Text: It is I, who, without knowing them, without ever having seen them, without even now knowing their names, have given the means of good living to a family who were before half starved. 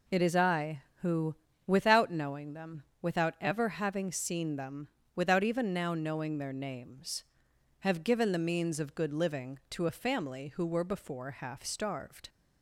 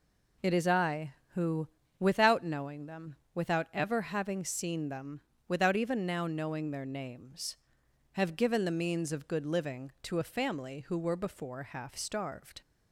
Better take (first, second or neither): neither